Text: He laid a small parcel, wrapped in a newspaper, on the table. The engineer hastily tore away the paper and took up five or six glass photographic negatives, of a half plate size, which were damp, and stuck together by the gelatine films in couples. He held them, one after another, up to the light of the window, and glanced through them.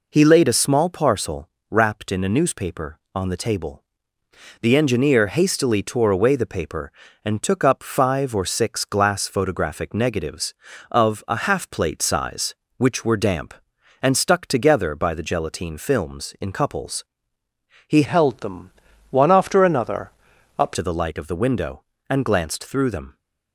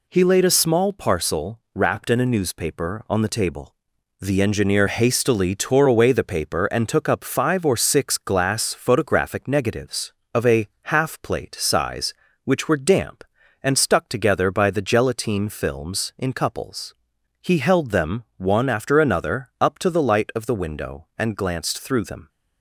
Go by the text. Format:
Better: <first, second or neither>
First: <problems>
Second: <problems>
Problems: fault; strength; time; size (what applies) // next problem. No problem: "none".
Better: second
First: changes voice from "held" to "up"; from 18.0 to 20.7 s; 2.7 s long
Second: none